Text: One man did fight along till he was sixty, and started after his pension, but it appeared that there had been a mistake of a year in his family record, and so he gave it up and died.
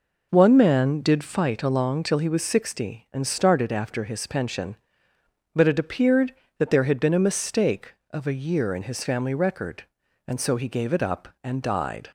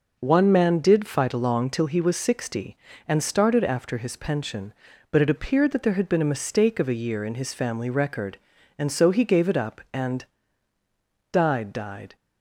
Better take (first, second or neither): first